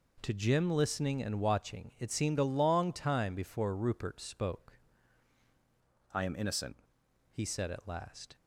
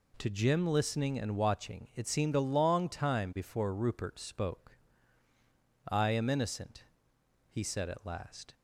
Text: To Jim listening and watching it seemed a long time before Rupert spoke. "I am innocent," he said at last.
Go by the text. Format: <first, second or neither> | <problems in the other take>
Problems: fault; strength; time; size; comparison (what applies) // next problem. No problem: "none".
second | changes voice from "I" to "innocent"; from 6.1 to 6.7 s; 0.6 s long